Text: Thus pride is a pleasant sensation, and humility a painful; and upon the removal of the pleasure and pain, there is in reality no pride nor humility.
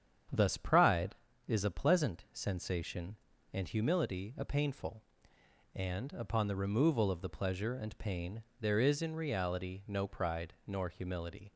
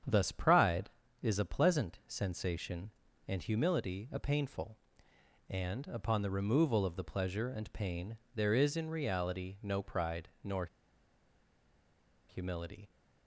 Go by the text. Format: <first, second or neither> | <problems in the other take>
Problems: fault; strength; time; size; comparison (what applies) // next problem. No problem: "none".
first | starts louder than the rest; strong; until 1.3 s; 8 dB; strong in the first // pauses between "nor" and "humility"; strong; at 10.6 s; 1.6 s long